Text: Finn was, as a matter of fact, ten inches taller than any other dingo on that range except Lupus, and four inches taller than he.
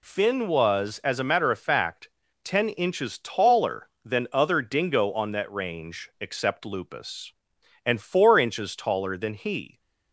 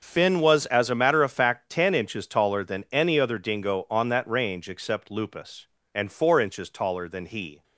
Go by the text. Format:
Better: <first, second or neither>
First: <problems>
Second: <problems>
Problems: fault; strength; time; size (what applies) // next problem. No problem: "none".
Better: second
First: skips "any"; at 4.3 s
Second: none